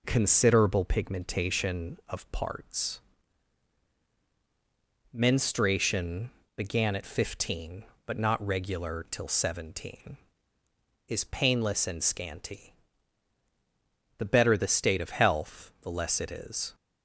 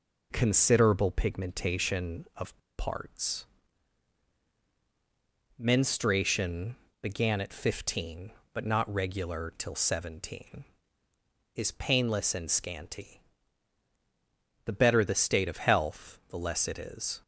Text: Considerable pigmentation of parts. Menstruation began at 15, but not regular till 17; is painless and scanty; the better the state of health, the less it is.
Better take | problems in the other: first | pauses between "of" and "parts"; slight; at 2.5 s; 0.20 s long // pauses between "Menstruation" and "began"; slight; at 6.7 s; 0.26 s long; slight in the first

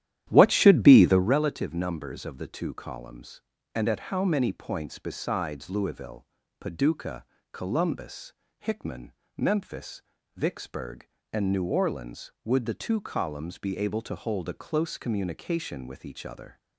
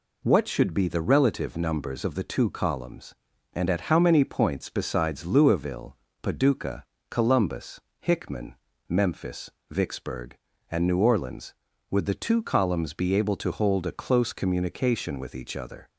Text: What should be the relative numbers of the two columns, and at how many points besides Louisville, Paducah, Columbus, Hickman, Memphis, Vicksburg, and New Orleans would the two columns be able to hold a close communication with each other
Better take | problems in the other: second | starts louder than the rest; strong; until 1.4 s; 11.5 dB

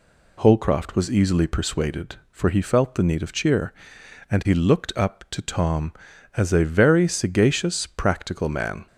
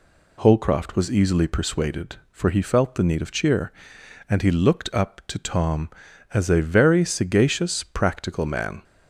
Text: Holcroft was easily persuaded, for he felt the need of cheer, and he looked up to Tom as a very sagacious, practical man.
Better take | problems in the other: neither | none

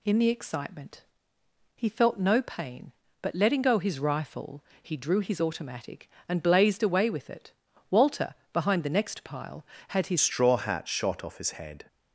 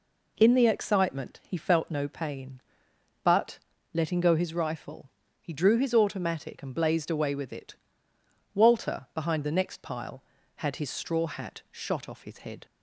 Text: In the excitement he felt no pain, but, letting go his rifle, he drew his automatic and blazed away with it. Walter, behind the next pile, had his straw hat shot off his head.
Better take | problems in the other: second | pauses between "excitement" and "he"; noticeable; at 1.0 s; 0.72 s long // changes voice at "straw"; from 10.2 s on; 1.6 s long

